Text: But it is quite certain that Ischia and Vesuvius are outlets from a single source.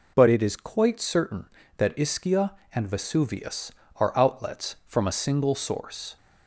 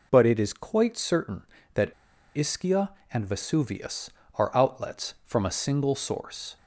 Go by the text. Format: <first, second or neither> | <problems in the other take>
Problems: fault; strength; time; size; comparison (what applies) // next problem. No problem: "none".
first | pauses between "that" and "Ischia"; at 1.9 s; 0.43 s long